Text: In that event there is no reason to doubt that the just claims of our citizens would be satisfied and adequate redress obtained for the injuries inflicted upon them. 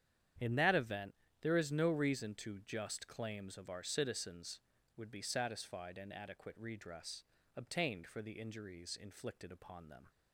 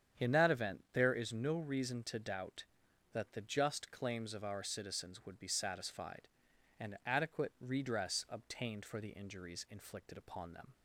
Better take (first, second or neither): second